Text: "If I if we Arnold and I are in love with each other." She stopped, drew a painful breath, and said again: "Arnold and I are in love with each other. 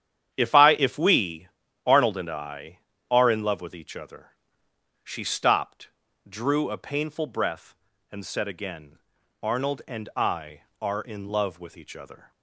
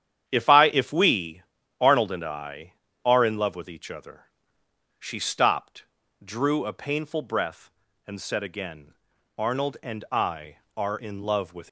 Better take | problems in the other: first | starts louder than the rest; strong; until 1.3 s; 9.5 dB; strong in the first // pauses between "we" and "Arnold"; slight; at 1.4 s; 0.36 s long; slight in the first // stops before "each other"; at 11.6 s

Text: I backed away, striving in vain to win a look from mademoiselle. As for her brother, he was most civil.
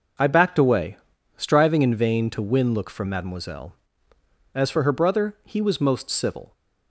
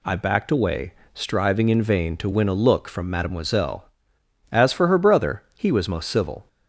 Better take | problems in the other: second | starts louder than the rest; noticeable; until 1.5 s; 6 dB // skips "a"; at 2.7 s

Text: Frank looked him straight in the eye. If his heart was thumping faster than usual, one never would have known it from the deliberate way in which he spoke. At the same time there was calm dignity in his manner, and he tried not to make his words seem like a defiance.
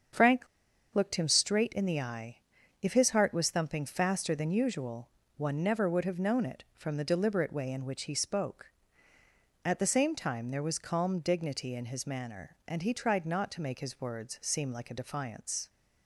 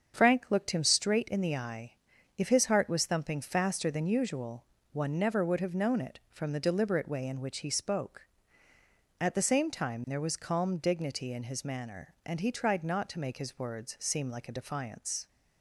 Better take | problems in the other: second | starts louder than the rest; strong; until 1.6 s; 7 dB; also in the second // pauses between "Frank" and "looked"; noticeable; at 0.4 s; 0.46 s long

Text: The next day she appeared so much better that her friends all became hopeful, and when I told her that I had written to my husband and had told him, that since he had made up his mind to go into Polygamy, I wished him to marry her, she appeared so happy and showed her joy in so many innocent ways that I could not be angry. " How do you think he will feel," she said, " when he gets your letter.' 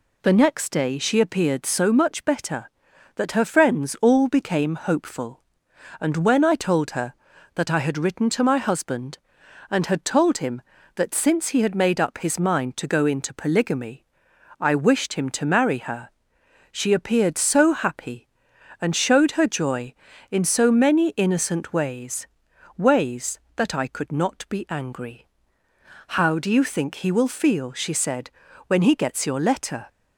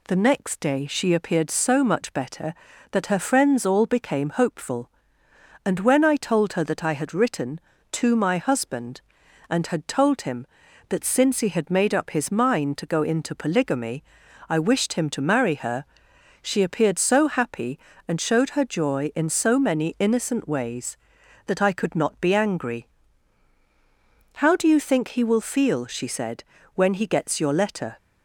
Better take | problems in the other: second | says "ways" twice; at 22.7 s

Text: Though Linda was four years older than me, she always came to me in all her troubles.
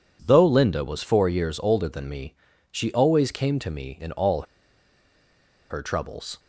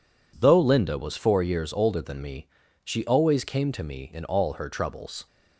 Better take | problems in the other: second | pauses between "all" and "her"; strong; at 4.4 s; 1.2 s long

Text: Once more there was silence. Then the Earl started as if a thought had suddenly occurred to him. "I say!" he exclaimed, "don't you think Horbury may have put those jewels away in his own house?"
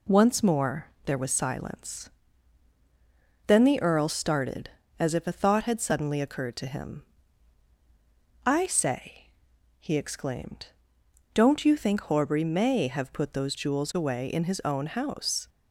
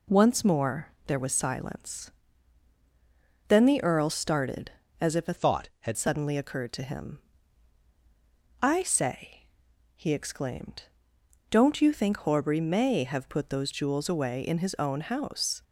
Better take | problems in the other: first | pauses between "more" and "there"; slight; at 0.8 s; 0.18 s long; slight in the first // changes voice from "thought" to "had"; from 5.3 to 5.9 s; 0.6 s long

